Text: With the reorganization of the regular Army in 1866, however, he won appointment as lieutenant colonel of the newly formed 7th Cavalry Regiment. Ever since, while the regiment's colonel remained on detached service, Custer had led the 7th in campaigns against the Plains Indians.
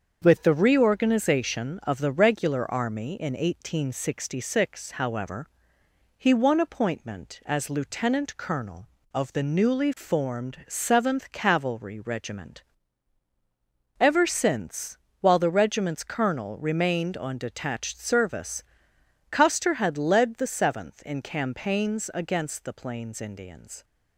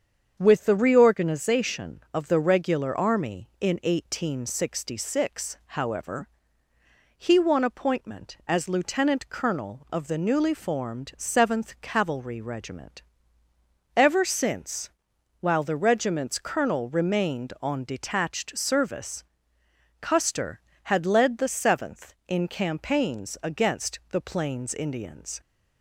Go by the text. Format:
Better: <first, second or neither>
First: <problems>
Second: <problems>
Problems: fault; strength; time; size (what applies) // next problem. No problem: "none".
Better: neither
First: starts louder than the rest; until 1.2 s; 7 dB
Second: starts louder than the rest; strong; until 1.4 s; 7.5 dB